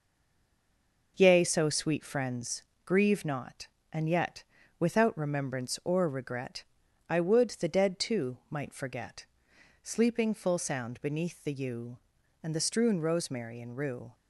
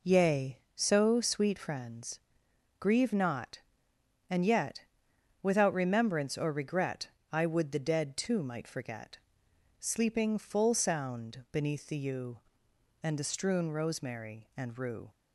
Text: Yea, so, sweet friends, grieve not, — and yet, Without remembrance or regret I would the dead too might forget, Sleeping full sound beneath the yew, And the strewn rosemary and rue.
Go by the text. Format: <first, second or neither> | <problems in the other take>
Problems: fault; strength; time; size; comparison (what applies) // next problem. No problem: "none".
second | stays silent before the first word; until 1.1 s; 1.1 s long // pauses between "regret" and "I"; at 6.6 s; 0.44 s long; slight in the second